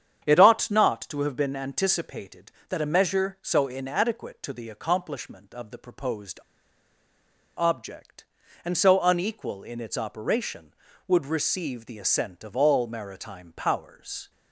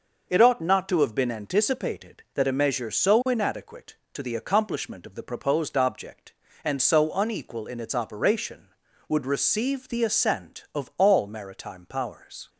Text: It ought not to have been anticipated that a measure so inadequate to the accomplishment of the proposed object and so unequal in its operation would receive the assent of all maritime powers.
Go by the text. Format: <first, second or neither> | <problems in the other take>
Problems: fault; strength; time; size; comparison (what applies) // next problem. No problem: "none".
second | starts louder than the rest; strong; until 1.2 s; 8 dB // pauses between "proposed" and "object"; at 6.3 s; 1.2 s long